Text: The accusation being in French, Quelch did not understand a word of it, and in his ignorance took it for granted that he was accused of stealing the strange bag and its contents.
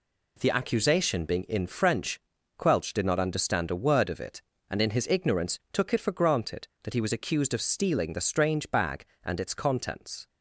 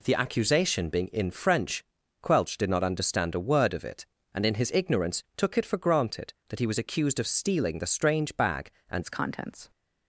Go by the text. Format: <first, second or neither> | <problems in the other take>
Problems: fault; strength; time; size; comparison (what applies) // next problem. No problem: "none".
first | changes voice at "its"; from 9.0 s on; 0.7 s long